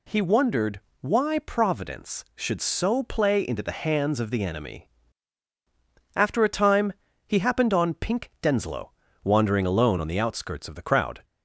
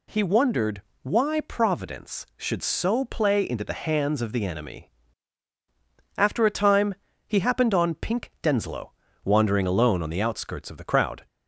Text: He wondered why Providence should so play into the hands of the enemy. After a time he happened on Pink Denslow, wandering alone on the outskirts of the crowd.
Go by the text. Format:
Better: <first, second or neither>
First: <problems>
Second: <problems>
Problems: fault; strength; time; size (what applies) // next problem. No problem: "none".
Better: neither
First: pauses between "wondered" and "why"; slight; at 0.7 s; 0.22 s long // pauses between "time" and "he"; slight; at 6.9 s; 0.32 s long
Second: pauses between "wondered" and "why"; slight; at 0.8 s; 0.22 s long // pauses between "time" and "he"; slight; at 6.9 s; 0.30 s long